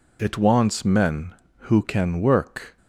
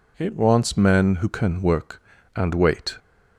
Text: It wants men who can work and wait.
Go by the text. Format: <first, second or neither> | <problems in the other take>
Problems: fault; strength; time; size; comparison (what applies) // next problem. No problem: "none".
second | stops before "and wait"; at 2.7 s